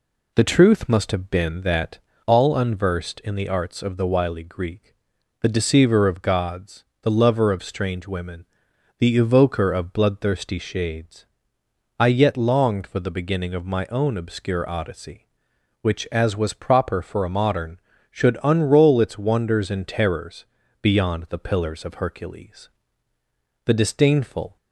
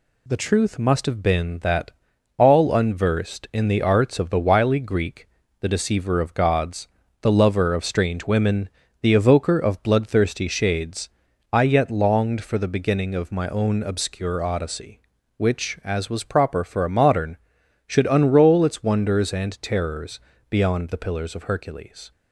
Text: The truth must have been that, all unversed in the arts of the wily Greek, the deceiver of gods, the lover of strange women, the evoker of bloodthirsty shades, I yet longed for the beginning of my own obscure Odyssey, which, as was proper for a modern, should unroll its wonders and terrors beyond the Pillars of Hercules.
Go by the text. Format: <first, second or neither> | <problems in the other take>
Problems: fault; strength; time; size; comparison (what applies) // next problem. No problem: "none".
second | pauses between "terrors" and "beyond"; slight; at 20.4 s; 0.36 s long; slight in the second // goes on to say "The disdainful"; noticeable; from 23.6 s on; 0.92 s long